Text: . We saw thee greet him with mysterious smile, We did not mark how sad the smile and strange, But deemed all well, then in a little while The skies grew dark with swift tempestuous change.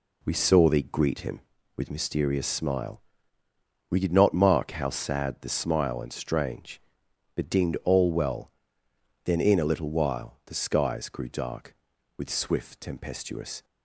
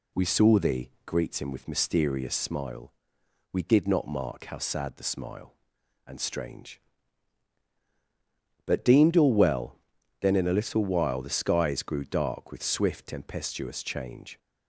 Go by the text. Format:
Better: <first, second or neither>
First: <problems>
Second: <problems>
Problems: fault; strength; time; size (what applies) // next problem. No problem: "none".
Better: second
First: stops before "change"; at 13.6 s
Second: none